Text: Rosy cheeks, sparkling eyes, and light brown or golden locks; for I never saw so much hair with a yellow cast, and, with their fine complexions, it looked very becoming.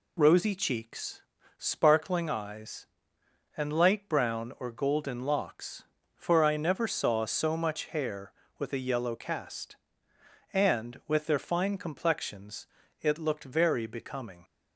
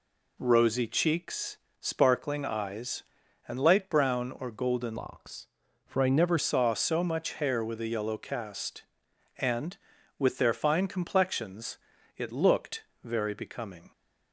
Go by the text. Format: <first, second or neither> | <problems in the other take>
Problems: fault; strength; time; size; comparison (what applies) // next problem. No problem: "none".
first | changes voice from "locks" to "never"; from 4.9 to 6.3 s; 1.4 s long // pauses between "looked" and "very"; slight; at 12.8 s; 0.20 s long